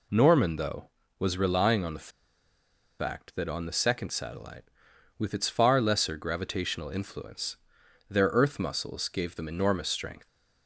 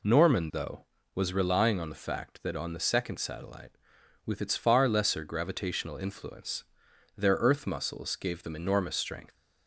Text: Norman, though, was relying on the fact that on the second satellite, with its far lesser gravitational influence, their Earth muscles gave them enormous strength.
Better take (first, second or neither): second